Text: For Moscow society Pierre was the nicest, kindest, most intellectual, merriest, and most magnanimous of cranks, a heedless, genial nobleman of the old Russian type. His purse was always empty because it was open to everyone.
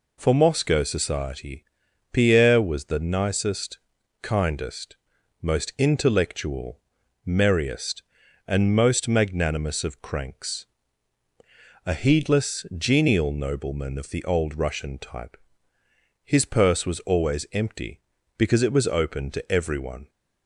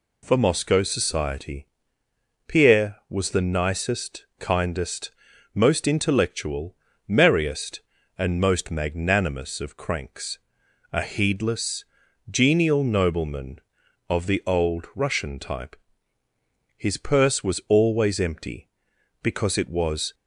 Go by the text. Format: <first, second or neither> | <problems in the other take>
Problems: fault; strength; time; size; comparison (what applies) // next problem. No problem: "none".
first | pauses between "society" and "Pierre"; noticeable; at 1.6 s; 0.82 s long; noticeable in the first // stops before "open to everyone"; at 20.1 s